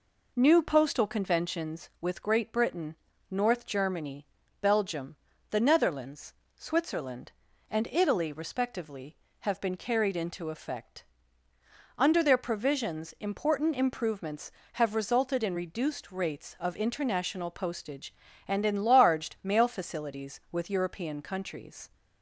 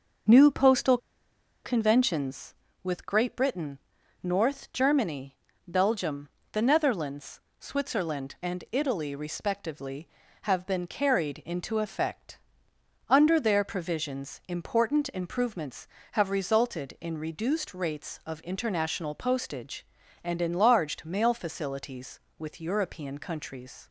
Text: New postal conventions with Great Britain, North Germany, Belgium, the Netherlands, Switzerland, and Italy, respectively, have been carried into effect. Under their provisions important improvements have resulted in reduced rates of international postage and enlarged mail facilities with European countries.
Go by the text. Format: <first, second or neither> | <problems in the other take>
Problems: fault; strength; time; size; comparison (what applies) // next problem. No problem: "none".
first | starts louder than the rest; until 1.9 s; 6 dB // pauses between "postal" and "conventions"; noticeable; at 0.9 s; 0.67 s long